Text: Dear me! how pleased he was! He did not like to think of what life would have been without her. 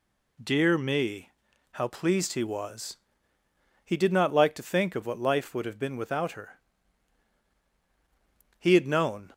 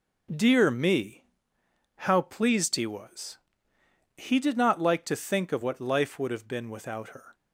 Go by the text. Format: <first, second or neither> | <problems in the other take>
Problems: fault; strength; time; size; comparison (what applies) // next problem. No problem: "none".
second | goes on to say "He had known"; noticeable; from 8.5 s on; 0.74 s long